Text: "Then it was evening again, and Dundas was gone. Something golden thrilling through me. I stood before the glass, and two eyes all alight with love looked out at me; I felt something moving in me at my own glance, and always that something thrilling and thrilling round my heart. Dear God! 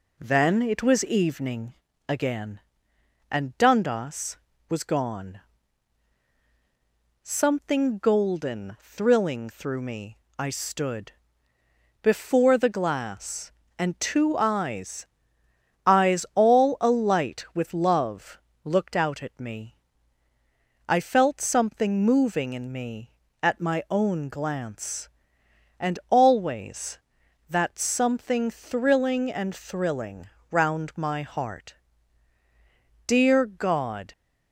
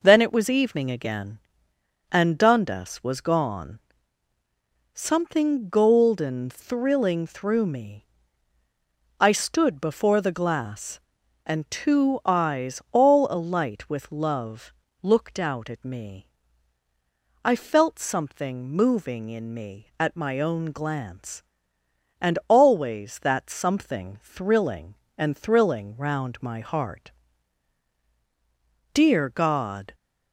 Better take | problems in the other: second | pauses between "evening" and "again"; slight; at 1.7 s; 0.34 s long // pauses between "stood" and "before"; noticeable; at 11.1 s; 0.90 s long // says "eyes" twice; at 15.8 s // pauses between "love" and "looked"; slight; at 18.3 s; 0.24 s long; slight in the second // pauses between "thrilling" and "round"; slight; at 30.2 s; 0.22 s long

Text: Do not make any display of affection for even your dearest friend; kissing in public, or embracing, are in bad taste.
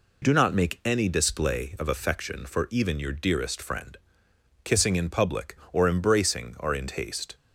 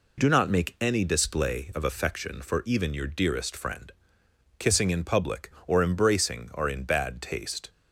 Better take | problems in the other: second | skips "bad"; at 6.8 s

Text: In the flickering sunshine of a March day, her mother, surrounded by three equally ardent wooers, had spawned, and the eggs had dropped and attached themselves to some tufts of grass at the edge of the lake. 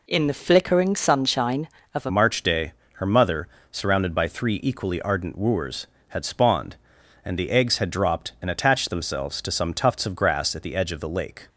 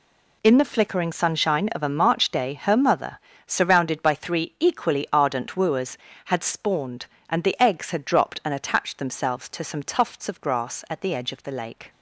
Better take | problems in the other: second | changes voice at "March"; from 2.1 s on; 9.3 s long

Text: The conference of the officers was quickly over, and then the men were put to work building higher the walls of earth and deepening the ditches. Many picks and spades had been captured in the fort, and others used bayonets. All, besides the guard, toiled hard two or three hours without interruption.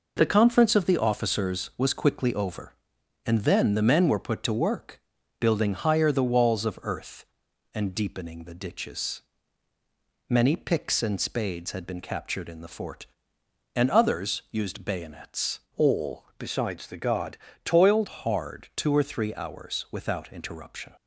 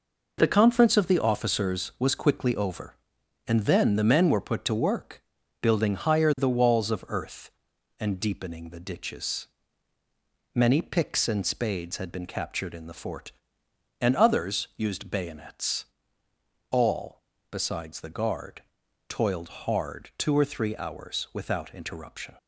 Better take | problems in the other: second | pauses between "work" and "building"; at 4.9 s; 0.38 s long; also in the second // changes voice from "All" to "toiled"; from 15.7 to 18.0 s; 2.3 s long

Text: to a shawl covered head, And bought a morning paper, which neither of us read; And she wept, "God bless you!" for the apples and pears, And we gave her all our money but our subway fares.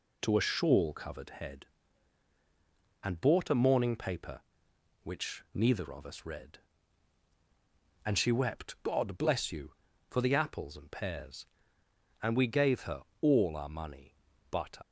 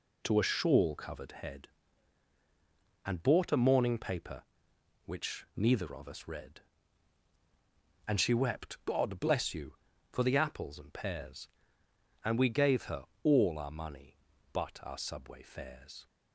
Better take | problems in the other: second | pauses between "her" and "all"; slight; at 13.0 s; 0.18 s long; slight in the second // stops before "our subway fares"; at 14.8 s

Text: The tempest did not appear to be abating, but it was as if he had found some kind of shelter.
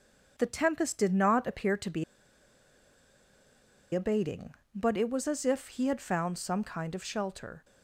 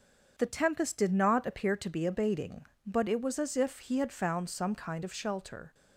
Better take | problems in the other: second | starts louder than the rest; until 1.3 s; 6.5 dB; also in the second // pauses between "be" and "abating"; strong; at 2.0 s; 1.9 s long

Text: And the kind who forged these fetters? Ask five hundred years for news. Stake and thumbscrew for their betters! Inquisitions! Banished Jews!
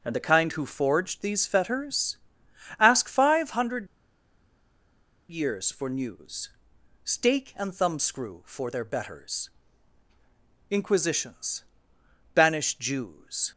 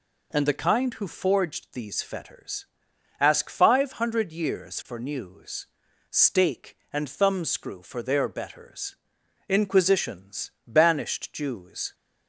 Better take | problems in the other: second | pauses between "hundred" and "years"; strong; at 3.8 s; 1.4 s long

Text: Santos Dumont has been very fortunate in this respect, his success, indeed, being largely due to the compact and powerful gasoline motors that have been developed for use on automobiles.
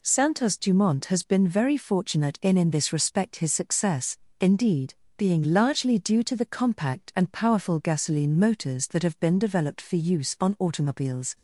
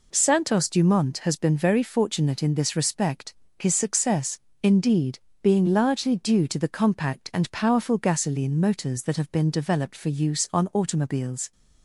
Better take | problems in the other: second | says "in" twice; at 2.5 s

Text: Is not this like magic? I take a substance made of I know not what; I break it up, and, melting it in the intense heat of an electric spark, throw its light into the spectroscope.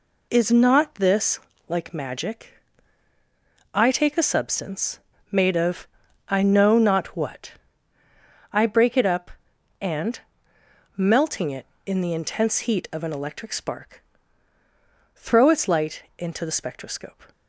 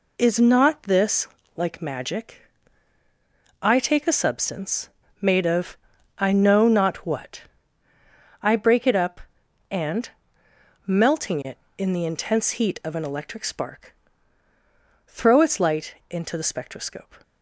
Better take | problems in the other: neither | pauses between "this" and "like"; slight; the same in both // pauses between "substance" and "made"; slight; the same in both // pauses between "of" and "I"; the same in both

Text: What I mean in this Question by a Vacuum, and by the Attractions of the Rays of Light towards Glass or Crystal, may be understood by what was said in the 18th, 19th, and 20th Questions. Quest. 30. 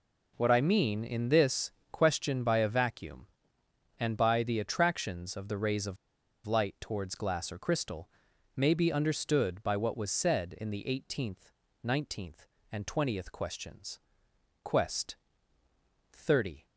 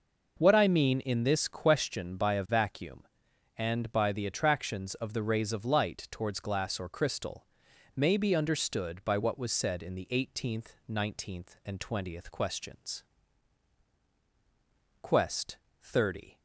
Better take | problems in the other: second | pauses between "this" and "Question"; slight; at 1.6 s; 0.22 s long // pauses between "of" and "Light"; noticeable; at 5.9 s; 0.50 s long

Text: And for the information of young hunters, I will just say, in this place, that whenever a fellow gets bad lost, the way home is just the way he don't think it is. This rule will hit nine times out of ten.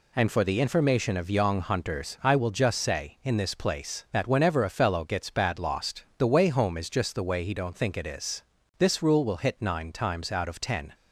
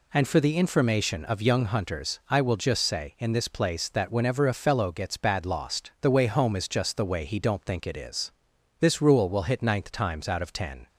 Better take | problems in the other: first | says "ninth" for "nine"; at 9.6 s

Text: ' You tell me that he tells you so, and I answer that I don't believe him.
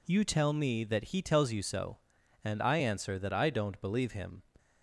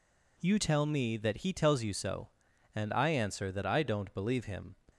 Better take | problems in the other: neither | none

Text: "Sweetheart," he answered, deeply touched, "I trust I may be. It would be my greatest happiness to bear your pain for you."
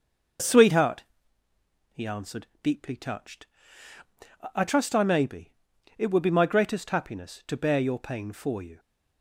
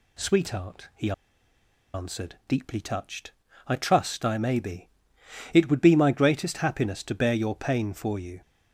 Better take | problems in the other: first | pauses between "he" and "answered"; noticeable; at 1.1 s; 0.82 s long

